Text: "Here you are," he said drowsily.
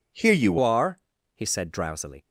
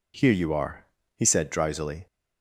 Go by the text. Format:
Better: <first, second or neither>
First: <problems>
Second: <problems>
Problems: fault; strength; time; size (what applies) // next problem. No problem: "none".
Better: second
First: changes voice at "are"; from 0.6 s on; 1.6 s long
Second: none